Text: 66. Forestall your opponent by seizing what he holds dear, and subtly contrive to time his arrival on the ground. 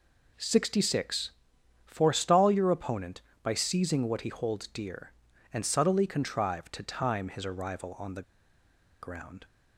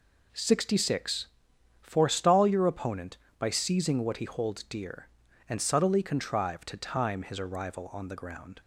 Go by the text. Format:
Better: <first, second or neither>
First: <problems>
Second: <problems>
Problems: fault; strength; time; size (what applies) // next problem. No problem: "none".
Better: second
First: pauses between "the" and "ground"; noticeable; at 8.2 s; 0.79 s long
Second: none